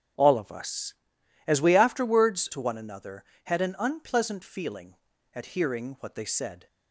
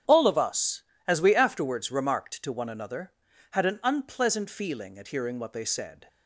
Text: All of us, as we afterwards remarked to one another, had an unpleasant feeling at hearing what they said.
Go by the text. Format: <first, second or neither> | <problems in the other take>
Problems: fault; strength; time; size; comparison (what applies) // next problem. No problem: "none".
second | starts louder than the rest; strong; until 1.7 s; 8.5 dB; strong in the second // skips "remarked"; at 2.4 s